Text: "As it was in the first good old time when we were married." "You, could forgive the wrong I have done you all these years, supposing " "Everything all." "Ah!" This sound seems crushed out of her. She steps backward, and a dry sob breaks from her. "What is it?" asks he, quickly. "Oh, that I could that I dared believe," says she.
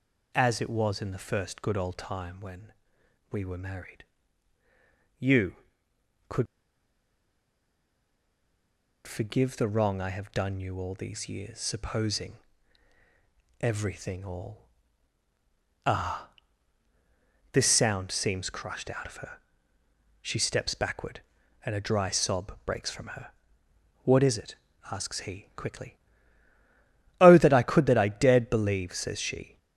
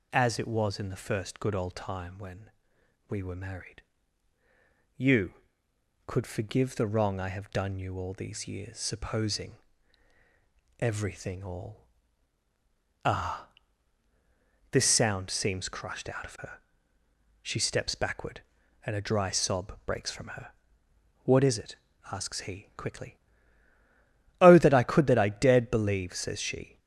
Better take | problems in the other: second | pauses between "when" and "we"; noticeable; at 2.7 s; 0.58 s long; noticeable in the second // pauses between "could" and "forgive"; strong; at 6.4 s; 2.6 s long

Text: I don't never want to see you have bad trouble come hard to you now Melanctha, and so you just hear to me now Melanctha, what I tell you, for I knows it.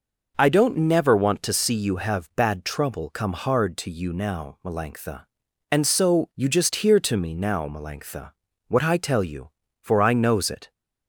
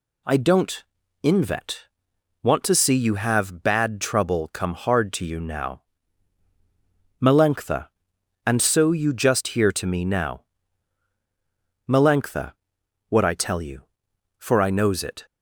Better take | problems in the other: first | says "invet" for "never"; at 1.2 s // pauses between "now" and "Melanctha"; strong; at 5.8 s; 1.3 s long // pauses between "now" and "Melanctha"; strong; at 10.4 s; 1.4 s long

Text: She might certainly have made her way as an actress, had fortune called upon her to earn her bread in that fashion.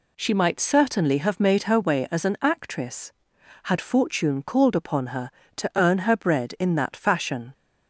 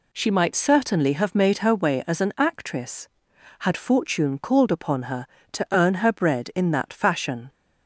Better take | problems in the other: neither | none

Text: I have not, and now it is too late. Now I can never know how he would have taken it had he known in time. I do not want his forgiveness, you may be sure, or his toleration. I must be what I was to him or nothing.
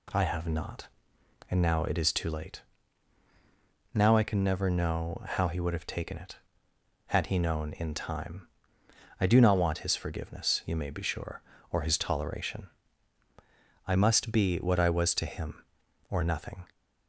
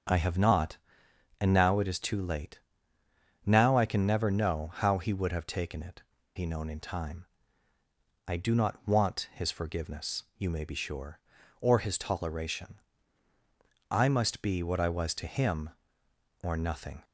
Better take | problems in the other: first | starts louder than the rest; strong; until 1.7 s; 7.5 dB // skips "had"; at 6.1 s

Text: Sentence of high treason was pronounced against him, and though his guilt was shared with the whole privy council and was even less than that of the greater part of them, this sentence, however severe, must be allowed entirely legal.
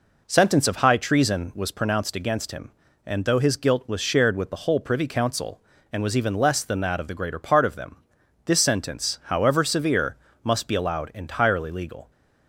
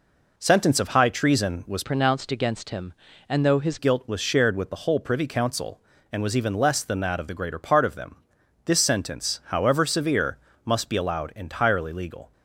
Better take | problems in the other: first | changes voice from "pronounced" to "his"; from 1.8 to 3.7 s; 1.9 s long

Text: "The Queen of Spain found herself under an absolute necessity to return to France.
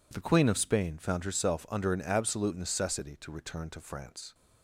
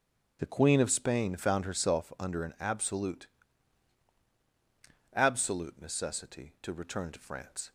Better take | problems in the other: first | starts louder than the rest; strong; until 1.4 s; 8.5 dB // says "absolute" twice; at 5.1 s

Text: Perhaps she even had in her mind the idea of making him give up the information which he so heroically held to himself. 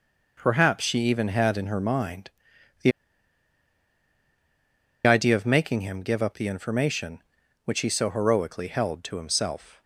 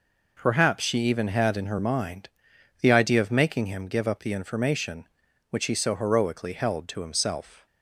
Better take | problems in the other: second | pauses between "mind" and "the"; noticeable; at 2.3 s; 0.52 s long; noticeable in the second // pauses between "the" and "idea"; strong; at 2.9 s; 2.1 s long

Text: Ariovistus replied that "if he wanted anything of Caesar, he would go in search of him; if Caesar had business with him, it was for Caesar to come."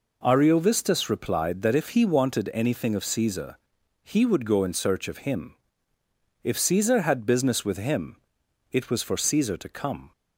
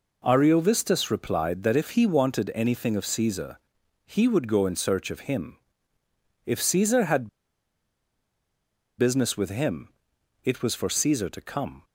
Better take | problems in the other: first | pauses between "had" and "business"; strong; at 7.2 s; 1.6 s long

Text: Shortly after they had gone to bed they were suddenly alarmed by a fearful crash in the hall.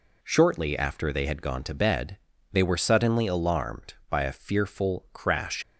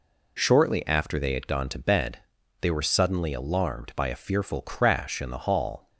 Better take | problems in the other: second | pauses between "bed" and "they"; slight; at 2.1 s; 0.36 s long; also in the second // stops before "in the hall"; at 5.6 s

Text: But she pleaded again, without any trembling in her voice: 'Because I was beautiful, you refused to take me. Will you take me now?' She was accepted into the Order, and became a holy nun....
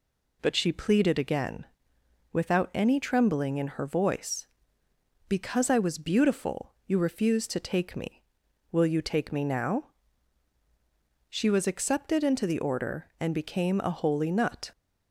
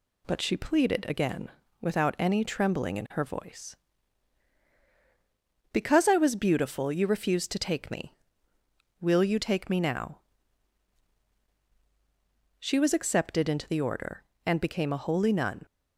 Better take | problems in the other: second | says "nut" for "nun"; at 14.2 s

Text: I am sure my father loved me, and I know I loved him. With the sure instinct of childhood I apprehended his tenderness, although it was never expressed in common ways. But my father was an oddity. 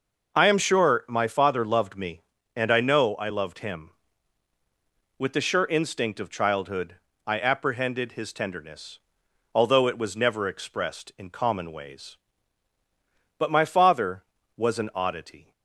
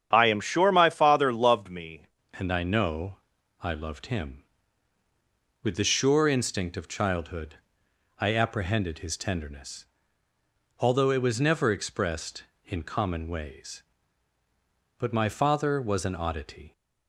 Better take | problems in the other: first | starts louder than the rest; strong; until 1.1 s; 9 dB // changes voice at "and"; from 2.3 s on; 14.4 s long // pauses between "know" and "I"; at 3.1 s; 0.44 s long // pauses between "childhood" and "I"; noticeable; at 7.5 s; 0.62 s long; slight in the first

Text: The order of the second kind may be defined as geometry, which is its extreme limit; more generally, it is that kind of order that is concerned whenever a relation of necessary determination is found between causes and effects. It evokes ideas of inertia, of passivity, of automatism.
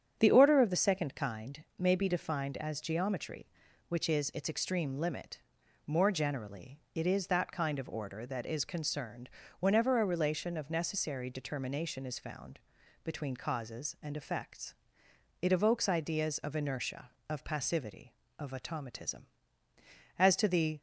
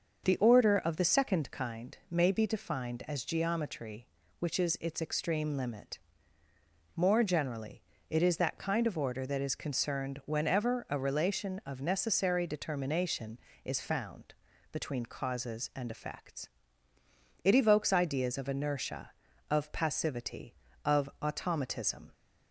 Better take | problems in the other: second | starts louder than the rest; strong; until 1.2 s; 8.5 dB; also in the second // pauses between "concerned" and "whenever"; slight; at 9.2 s; 0.30 s long // pauses between "found" and "between"; noticeable; at 12.5 s; 0.46 s long; also in the second // goes on to say "As to the"; noticeable; from 20.1 s on; 0.62 s long

